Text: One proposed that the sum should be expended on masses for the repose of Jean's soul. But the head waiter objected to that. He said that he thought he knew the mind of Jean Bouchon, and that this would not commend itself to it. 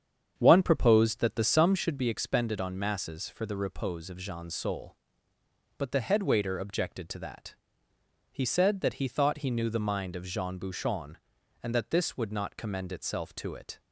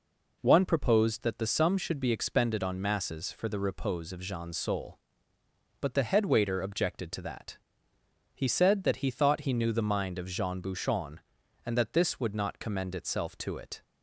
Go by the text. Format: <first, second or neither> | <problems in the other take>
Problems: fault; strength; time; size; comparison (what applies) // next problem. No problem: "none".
second | starts louder than the rest; strong; until 2.0 s; 8 dB